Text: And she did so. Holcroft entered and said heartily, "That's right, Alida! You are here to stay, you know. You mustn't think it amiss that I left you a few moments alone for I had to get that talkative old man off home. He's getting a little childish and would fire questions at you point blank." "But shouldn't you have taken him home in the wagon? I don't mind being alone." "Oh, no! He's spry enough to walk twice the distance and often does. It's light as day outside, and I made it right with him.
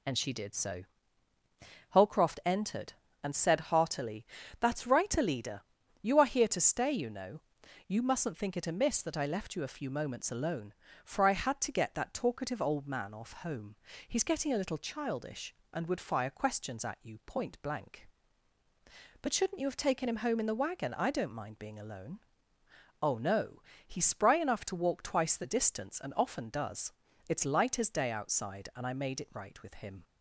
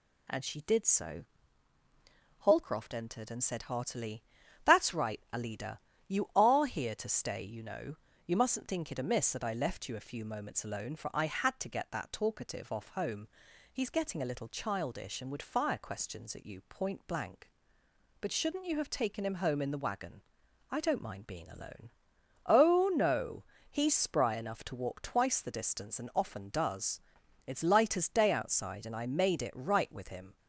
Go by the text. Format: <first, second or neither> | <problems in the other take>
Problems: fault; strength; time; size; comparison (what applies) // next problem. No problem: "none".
first | skips "old man"; at 12.7 s